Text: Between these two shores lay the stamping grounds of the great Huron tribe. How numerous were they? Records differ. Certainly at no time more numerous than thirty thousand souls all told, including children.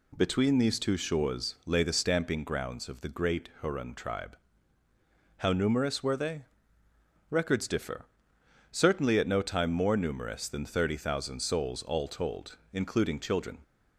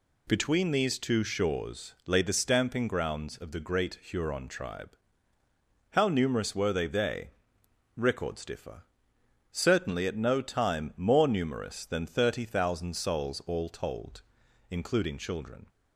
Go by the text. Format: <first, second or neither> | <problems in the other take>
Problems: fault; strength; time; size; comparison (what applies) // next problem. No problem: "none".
first | says "they" twice; at 6.8 s